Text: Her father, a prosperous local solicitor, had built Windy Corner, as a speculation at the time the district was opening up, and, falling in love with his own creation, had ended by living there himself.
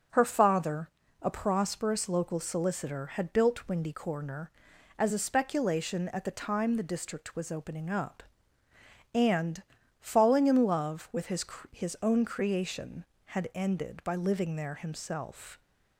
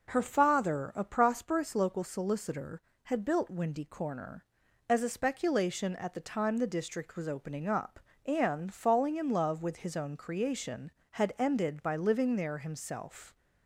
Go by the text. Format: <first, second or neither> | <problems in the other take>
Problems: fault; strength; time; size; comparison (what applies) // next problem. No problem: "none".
second | says "his" twice; at 11.7 s